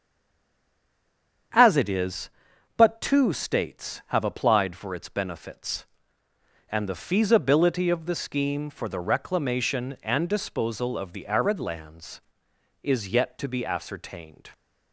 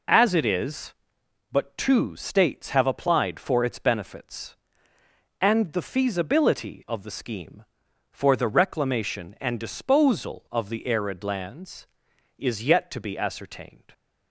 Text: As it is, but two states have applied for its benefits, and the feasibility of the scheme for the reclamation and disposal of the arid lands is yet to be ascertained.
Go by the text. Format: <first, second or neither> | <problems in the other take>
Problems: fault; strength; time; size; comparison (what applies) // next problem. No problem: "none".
second | stays silent before the first word; noticeable; until 1.5 s; 1.5 s long // starts louder than the rest; strong; until 3.0 s; 8 dB